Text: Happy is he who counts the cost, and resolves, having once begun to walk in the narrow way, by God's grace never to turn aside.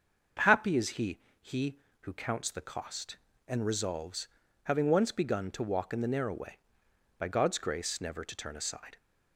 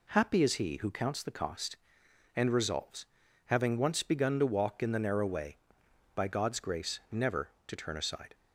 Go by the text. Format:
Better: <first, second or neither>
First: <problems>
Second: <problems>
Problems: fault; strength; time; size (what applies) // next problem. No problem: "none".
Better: second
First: starts louder than the rest; until 1.6 s; 6.5 dB // says "he" twice; at 1.4 s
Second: none